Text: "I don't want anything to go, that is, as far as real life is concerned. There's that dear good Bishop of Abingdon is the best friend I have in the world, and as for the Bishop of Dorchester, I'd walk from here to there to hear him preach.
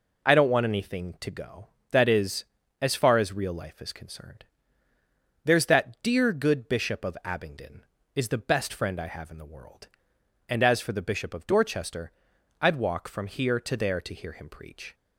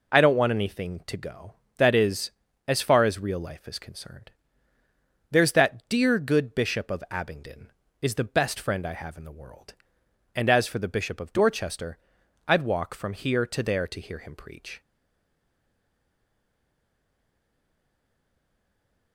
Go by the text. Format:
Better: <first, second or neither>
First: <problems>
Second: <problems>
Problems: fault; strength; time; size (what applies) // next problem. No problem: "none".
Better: first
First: none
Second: stays silent after the last word; strong; from 14.8 s on; 4.3 s long